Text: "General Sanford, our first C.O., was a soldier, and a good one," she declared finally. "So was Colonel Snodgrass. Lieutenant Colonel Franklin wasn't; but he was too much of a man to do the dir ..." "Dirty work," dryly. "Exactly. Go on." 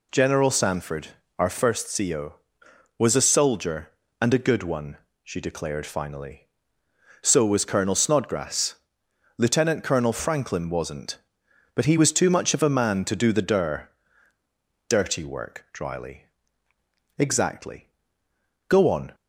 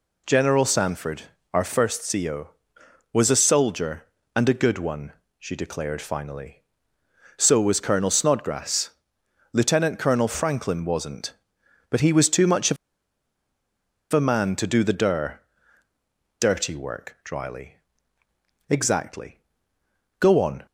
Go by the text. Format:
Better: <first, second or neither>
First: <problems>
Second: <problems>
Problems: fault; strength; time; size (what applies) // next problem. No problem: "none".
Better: first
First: none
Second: pauses between "of" and "a"; strong; at 12.7 s; 1.3 s long